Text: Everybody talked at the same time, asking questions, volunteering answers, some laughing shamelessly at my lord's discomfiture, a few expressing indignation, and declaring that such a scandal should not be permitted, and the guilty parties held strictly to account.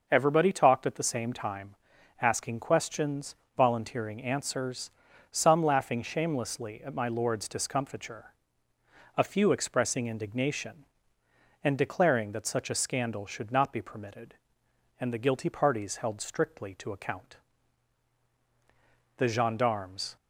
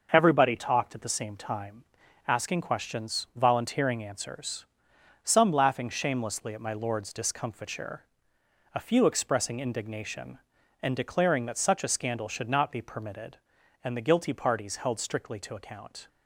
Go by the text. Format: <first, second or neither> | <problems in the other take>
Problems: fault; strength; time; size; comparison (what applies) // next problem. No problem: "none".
second | starts louder than the rest; noticeable; until 1.1 s; 6 dB; also in the second // goes on to say "The gendarmes"; noticeable; from 19.1 s on; 0.98 s long